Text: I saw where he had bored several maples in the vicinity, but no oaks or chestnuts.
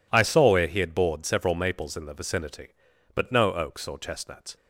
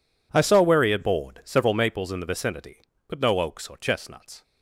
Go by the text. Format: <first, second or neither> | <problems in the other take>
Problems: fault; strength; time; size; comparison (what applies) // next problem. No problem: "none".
neither | none